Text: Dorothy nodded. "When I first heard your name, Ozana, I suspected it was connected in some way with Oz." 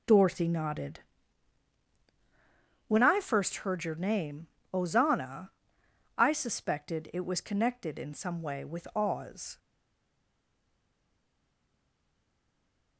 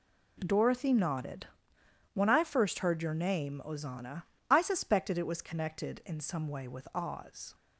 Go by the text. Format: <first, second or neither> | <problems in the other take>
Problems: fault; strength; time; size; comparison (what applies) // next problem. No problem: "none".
second | stays silent after the last word; strong; from 9.5 s on; 3.4 s long